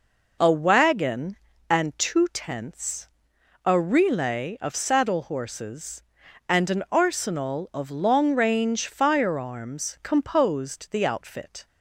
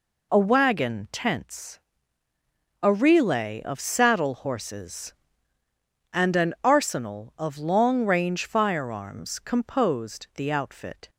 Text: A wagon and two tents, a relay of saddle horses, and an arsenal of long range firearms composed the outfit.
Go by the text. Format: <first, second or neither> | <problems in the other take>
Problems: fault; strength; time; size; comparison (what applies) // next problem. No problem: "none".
first | skips "and two"; at 1.0 s